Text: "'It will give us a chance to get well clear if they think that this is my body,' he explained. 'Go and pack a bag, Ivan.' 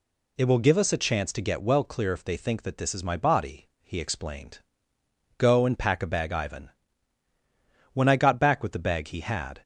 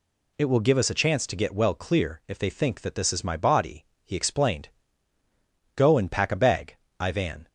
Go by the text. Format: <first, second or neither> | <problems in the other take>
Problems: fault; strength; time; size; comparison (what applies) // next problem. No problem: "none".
second | goes on to say "When I got back with the bag he had"; strong; from 7.9 s on; 1.6 s long